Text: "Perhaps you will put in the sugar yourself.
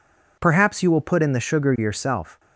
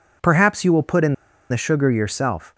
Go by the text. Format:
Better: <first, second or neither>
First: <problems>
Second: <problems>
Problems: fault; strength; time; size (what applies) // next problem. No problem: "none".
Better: first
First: none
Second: pauses between "in" and "the"; at 1.1 s; 0.36 s long